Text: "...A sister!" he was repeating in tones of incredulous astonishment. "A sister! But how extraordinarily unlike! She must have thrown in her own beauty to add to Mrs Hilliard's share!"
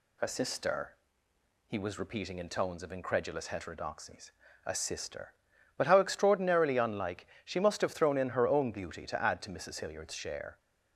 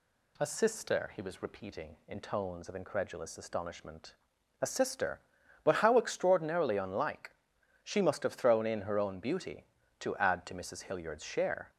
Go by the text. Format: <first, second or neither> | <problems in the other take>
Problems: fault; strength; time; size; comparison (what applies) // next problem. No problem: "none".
second | says "heterodoxies" for "astonishment"; at 3.4 s